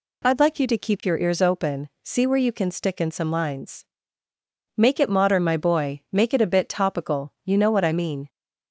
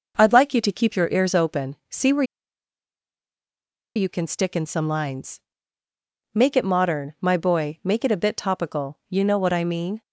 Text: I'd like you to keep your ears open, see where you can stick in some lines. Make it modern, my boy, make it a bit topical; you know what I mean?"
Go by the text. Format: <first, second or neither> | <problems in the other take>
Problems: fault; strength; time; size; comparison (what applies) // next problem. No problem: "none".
first | pauses between "where" and "you"; strong; at 2.2 s; 1.7 s long